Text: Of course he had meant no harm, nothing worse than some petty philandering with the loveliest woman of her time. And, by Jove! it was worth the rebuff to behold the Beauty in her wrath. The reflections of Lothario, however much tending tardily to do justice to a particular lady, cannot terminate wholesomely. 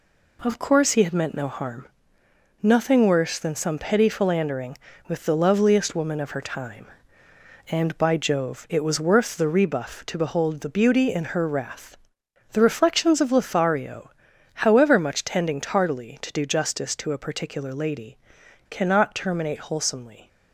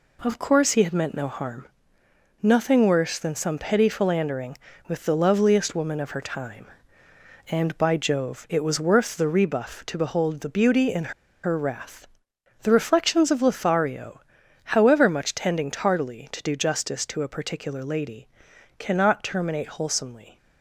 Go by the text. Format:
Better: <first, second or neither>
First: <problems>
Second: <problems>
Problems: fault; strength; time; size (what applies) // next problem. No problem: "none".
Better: first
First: none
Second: pauses between "in" and "her"; slight; at 11.1 s; 0.33 s long